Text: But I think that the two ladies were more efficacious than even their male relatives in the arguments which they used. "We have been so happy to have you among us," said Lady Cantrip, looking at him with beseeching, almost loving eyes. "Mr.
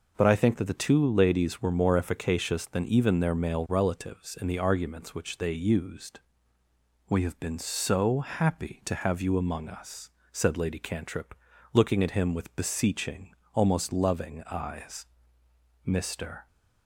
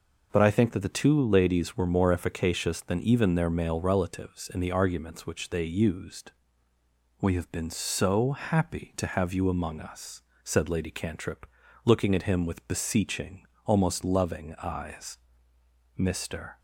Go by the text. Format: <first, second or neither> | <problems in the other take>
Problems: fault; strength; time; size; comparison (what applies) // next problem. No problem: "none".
neither | none